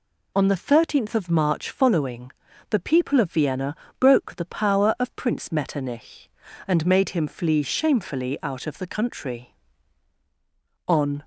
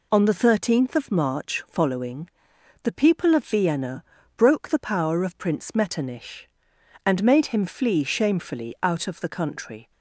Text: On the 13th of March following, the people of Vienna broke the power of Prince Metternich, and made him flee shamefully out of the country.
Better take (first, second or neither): second